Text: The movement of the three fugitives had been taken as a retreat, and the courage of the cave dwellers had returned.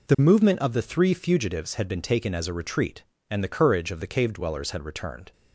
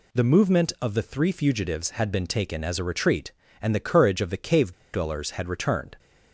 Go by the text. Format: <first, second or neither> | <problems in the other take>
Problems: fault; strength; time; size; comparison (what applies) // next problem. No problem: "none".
first | pauses between "cave" and "dwellers"; slight; at 4.7 s; 0.20 s long